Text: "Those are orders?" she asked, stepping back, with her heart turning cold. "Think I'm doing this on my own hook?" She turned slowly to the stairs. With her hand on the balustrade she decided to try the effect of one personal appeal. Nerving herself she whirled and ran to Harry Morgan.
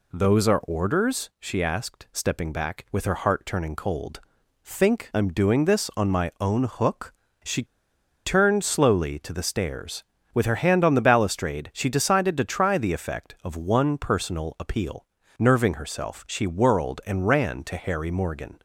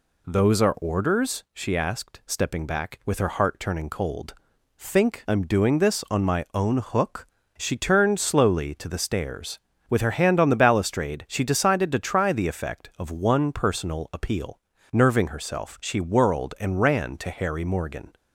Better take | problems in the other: second | pauses between "She" and "turned"; noticeable; at 7.6 s; 0.61 s long

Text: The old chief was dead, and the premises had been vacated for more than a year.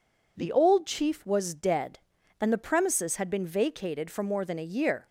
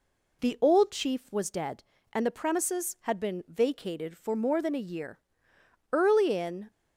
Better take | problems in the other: first | goes on to say "Early in"; noticeable; from 5.9 s on; 0.78 s long

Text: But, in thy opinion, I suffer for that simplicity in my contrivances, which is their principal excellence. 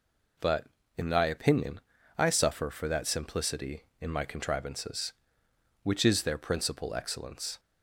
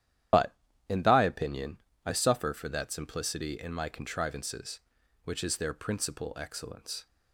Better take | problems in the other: first | loses the start of "But"; at 0.3 s; 90 ms // starts louder than the rest; strong; until 1.6 s; 11 dB

